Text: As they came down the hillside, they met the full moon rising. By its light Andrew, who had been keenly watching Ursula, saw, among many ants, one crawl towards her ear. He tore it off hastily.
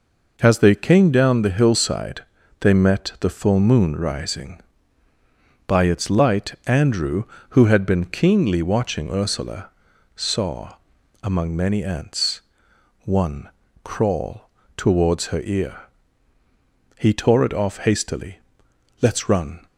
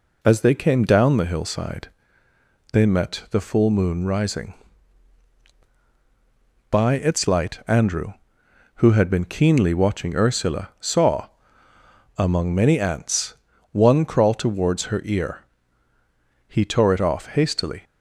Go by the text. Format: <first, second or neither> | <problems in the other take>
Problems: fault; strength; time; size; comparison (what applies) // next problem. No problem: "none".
second | pauses between "one" and "crawl"; slight; at 13.4 s; 0.34 s long // pauses between "crawl" and "towards"; slight; at 14.4 s; 0.26 s long // goes on to say "Let's run"; noticeable; from 18.9 s on; 0.66 s long